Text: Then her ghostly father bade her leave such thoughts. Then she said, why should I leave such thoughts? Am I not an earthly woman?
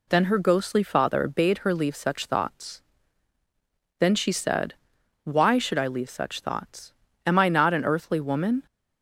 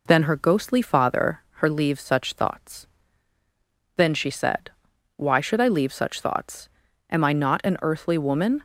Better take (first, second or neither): first